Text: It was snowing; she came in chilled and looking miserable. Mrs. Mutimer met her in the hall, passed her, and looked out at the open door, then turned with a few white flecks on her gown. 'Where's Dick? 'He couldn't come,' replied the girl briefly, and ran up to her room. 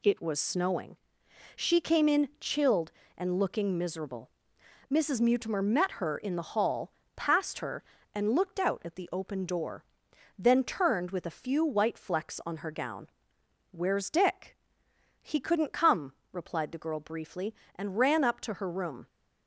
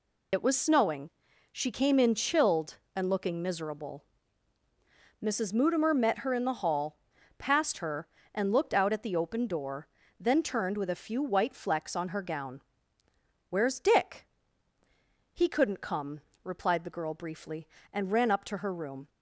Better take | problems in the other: first | loses the start of "It"; at 0.3 s; 45 ms

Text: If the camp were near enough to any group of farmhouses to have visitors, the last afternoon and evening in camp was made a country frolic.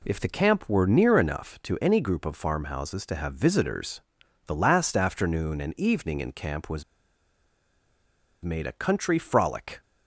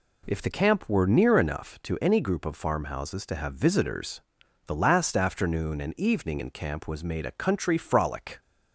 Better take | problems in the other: second | pauses between "was" and "made"; strong; at 6.8 s; 1.6 s long

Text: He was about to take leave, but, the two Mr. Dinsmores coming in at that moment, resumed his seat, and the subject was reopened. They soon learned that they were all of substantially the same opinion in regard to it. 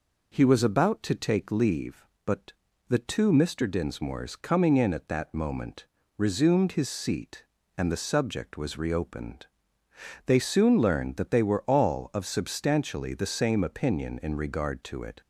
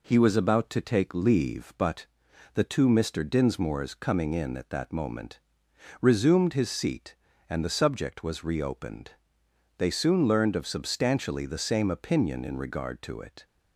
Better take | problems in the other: first | skips "that they were all"; at 10.5 s

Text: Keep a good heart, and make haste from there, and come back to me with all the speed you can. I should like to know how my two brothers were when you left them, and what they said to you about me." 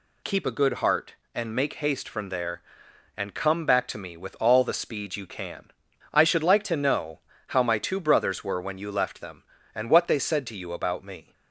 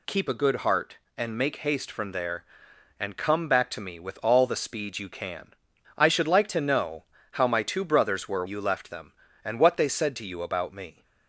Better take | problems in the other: first | pauses between "know" and "how"; slight; at 7.0 s; 0.30 s long; slight in the first // skips "when"; at 8.4 s

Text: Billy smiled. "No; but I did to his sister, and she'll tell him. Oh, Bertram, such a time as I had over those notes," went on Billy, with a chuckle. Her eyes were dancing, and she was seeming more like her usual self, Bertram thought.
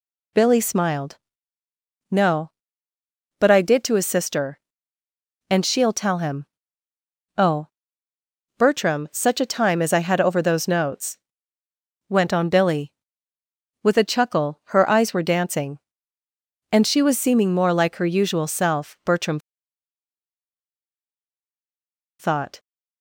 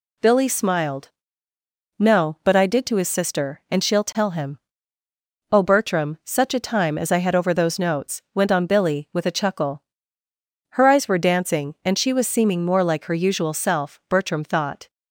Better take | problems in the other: second | pauses between "Bertram" and "thought"; strong; at 19.3 s; 2.8 s long

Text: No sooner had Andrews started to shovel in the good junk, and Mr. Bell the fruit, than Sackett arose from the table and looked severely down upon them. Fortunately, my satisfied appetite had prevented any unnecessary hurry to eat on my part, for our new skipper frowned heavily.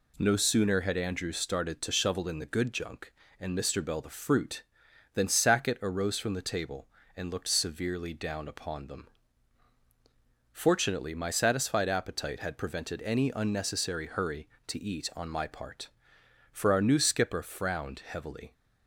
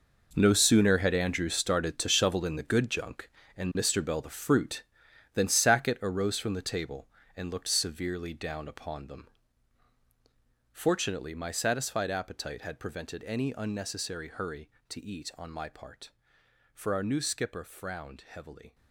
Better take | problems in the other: first | gets quieter; strong; throughout; 13.5 dB

